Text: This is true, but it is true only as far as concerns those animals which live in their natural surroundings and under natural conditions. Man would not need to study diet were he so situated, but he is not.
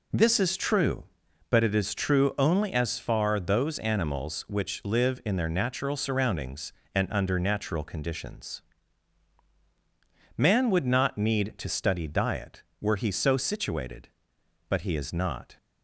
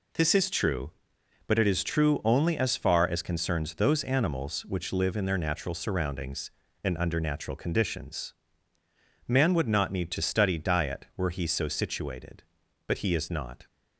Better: second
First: skips "as concerns"; at 3.3 s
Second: none

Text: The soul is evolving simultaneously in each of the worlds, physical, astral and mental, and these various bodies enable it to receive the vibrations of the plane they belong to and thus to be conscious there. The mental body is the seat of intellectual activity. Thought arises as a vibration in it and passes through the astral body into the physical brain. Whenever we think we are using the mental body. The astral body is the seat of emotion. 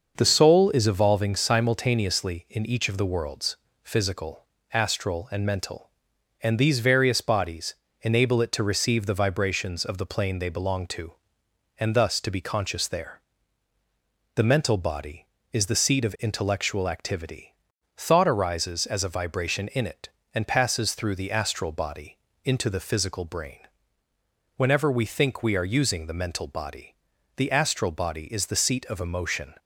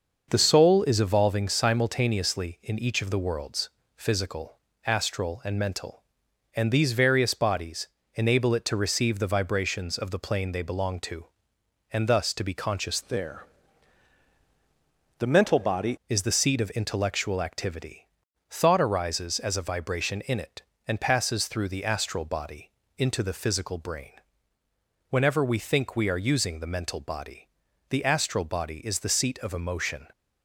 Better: first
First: starts louder than the rest; until 1.1 s; 6.5 dB // pauses between "bodies" and "enable"; slight; at 7.7 s; 0.26 s long // pauses between "body" and "into"; slight; at 22.1 s; 0.26 s long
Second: starts louder than the rest; until 1.3 s; 6.5 dB // pauses between "bodies" and "enable"; slight; at 7.8 s; 0.26 s long // changes voice from "there" to "body"; from 13.0 to 15.9 s; 2.9 s long // pauses between "body" and "into"; slight; at 22.7 s; 0.26 s long

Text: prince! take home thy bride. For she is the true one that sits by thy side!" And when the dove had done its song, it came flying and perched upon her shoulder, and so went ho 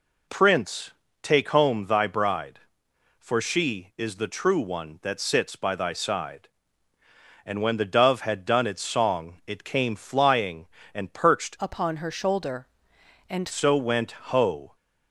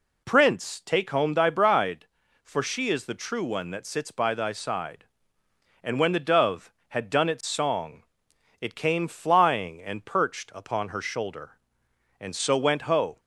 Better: second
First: changes voice from "upon" to "and"; from 11.5 to 13.4 s; 1.9 s long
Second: none

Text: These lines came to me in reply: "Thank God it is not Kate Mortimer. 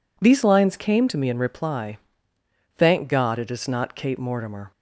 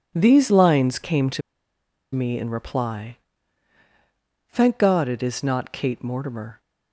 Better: first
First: none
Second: pauses between "to" and "me"; noticeable; at 1.4 s; 0.73 s long

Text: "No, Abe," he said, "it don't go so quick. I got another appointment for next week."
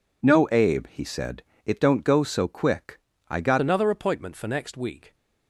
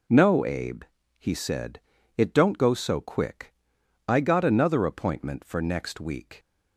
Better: second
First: changes voice at "another"; from 3.6 s on; 1.5 s long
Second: none

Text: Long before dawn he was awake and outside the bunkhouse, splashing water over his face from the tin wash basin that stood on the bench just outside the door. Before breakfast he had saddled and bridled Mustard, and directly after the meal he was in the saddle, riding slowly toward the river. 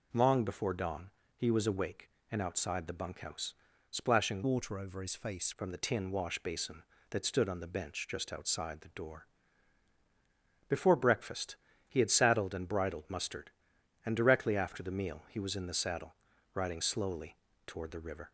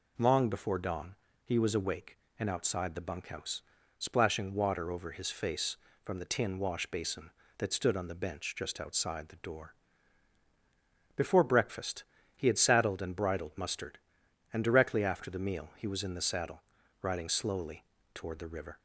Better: second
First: pauses between "dawn" and "he"; slight; at 1.1 s; 0.26 s long // changes voice from "water" to "face"; from 4.4 to 5.5 s; 1.1 s long // pauses between "breakfast" and "he"; slight; at 11.5 s; 0.32 s long // pauses between "slowly" and "toward"; slight; at 17.3 s; 0.28 s long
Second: pauses between "dawn" and "he"; slight; at 1.1 s; 0.29 s long // pauses between "breakfast" and "he"; slight; at 12.0 s; 0.32 s long // pauses between "slowly" and "toward"; slight; at 17.8 s; 0.28 s long

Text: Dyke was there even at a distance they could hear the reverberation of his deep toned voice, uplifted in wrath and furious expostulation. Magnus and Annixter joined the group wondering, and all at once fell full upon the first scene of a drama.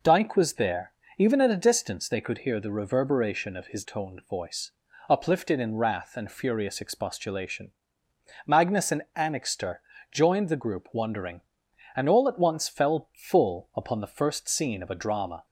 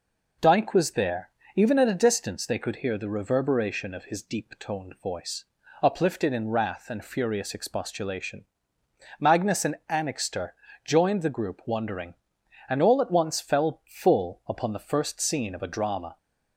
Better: second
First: pauses between "there" and "even"; slight; at 0.9 s; 0.28 s long // skips "deep"; at 3.8 s // pauses between "Annixter" and "joined"; slight; at 9.8 s; 0.30 s long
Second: pauses between "there" and "even"; slight; at 1.3 s; 0.28 s long // pauses between "Annixter" and "joined"; slight; at 10.5 s; 0.30 s long

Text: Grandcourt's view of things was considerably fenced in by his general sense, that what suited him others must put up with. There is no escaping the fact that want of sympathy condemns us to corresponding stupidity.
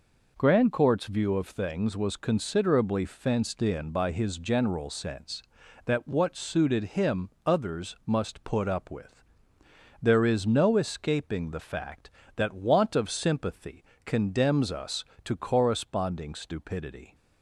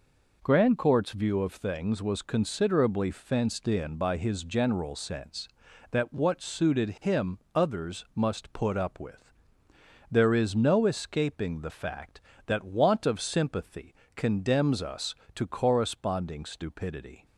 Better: neither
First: pauses between "him" and "others"; slight; at 7.3 s; 0.16 s long // pauses between "sympathy" and "condemns"; slight; at 13.8 s; 0.22 s long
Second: pauses between "him" and "others"; slight; at 7.3 s; 0.16 s long // pauses between "sympathy" and "condemns"; slight; at 13.9 s; 0.22 s long

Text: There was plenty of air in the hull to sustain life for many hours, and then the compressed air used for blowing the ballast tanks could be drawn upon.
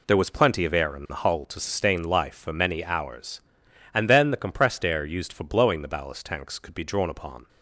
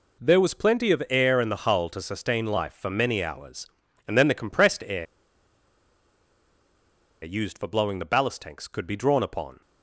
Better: first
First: none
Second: pauses between "air" and "used"; strong; at 5.0 s; 2.1 s long

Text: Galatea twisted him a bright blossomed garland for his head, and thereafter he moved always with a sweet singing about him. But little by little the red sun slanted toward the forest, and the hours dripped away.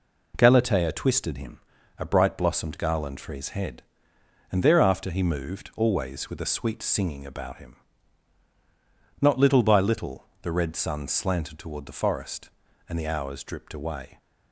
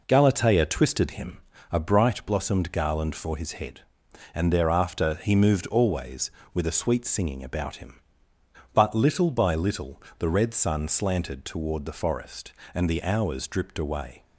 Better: second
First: pauses between "him" and "a"; at 1.5 s; 0.38 s long // says "Not" for "But"; at 9.2 s // pauses between "little" and "the"; slight; at 10.2 s; 0.16 s long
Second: pauses between "him" and "a"; slight; at 1.3 s; 0.34 s long // pauses between "little" and "the"; slight; at 10.0 s; 0.16 s long

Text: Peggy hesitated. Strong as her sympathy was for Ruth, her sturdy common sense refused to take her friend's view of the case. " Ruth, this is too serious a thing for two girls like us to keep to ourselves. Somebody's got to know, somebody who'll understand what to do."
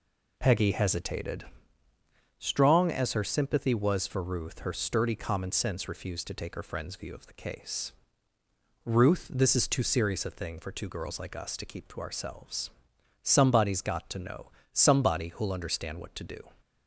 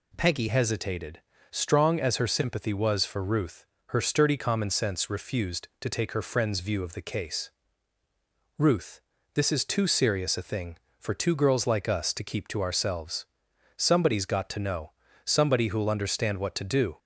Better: first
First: none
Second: changes voice at "hesitated"; from 0.4 s on; 16.5 s long

